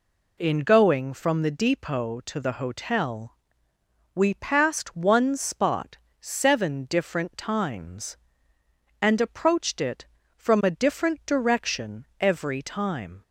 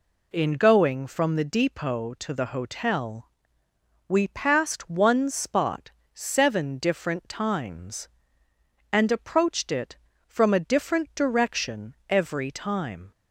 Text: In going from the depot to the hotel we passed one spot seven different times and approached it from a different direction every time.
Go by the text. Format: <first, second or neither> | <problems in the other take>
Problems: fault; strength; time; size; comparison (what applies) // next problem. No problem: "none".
neither | pauses between "hotel" and "we"; noticeable; the same in both // pauses between "spot" and "seven"; slight; the same in both